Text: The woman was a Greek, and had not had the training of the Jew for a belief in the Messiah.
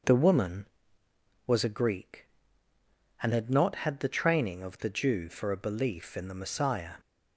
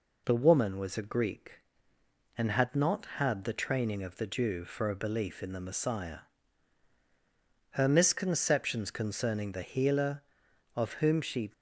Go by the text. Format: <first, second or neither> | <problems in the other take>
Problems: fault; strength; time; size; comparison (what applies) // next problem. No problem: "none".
first | goes on to say "Her misconceptions concerning the healer of whom she"; strong; from 7.7 s on; 3.8 s long